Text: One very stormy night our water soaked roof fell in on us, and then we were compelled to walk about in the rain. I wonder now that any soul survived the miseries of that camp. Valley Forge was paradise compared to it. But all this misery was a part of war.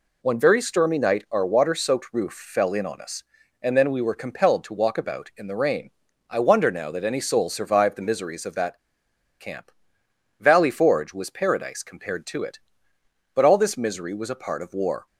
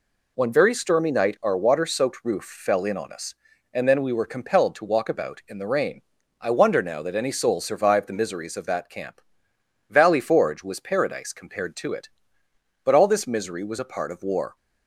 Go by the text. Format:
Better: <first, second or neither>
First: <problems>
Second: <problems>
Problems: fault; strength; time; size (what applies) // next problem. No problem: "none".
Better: second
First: pauses between "that" and "camp"; noticeable; at 8.7 s; 0.61 s long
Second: none